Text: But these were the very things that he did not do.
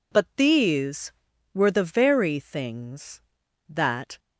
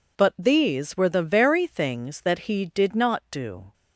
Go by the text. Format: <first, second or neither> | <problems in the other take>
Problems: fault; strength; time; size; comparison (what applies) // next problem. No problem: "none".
second | stops before "he did not do"; at 4.1 s